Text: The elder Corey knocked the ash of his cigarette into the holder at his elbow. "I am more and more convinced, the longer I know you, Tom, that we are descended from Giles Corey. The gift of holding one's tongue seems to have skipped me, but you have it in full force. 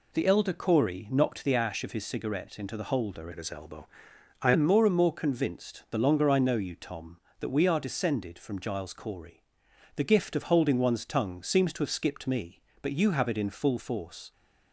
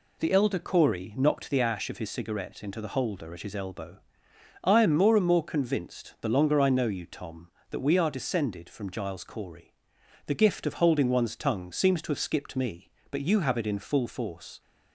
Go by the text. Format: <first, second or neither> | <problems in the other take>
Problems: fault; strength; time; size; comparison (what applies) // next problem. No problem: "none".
second | changes voice from "at" to "I"; from 3.3 to 4.5 s; 1.2 s long